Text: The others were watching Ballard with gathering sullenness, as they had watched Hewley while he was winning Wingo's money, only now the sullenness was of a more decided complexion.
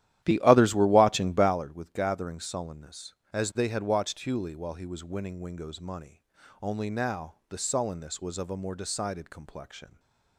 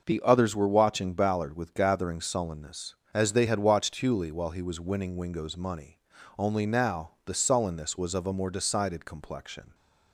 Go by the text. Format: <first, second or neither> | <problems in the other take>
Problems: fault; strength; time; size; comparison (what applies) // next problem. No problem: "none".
second | starts louder than the rest; strong; until 1.6 s; 12.5 dB // stays silent after the last word; slight; from 9.8 s on; 0.5 s long